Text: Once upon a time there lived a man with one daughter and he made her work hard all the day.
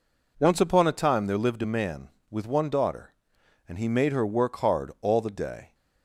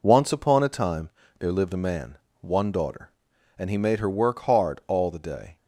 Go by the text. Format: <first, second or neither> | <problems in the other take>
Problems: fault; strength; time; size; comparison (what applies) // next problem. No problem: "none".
first | pauses between "time" and "there"; slight; at 1.0 s; 0.30 s long // skips "with"; at 2.2 s